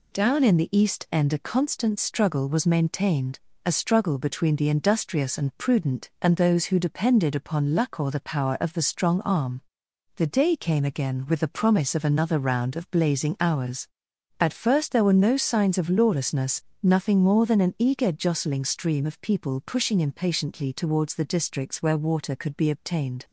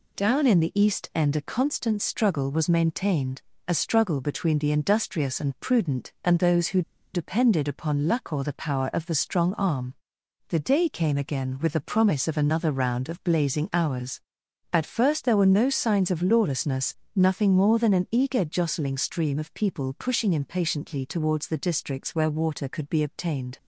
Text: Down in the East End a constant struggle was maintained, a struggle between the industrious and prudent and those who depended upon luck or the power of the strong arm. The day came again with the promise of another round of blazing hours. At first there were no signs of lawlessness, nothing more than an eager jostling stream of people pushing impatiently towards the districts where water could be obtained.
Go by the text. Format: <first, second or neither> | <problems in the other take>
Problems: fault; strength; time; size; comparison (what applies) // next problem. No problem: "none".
first | pauses between "who" and "depended"; slight; at 6.8 s; 0.33 s long